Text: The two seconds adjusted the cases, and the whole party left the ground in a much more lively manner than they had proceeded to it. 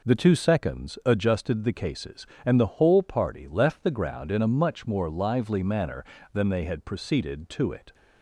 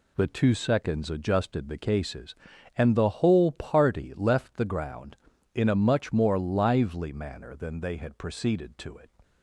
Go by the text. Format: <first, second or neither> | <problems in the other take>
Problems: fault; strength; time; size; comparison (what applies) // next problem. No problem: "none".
neither | none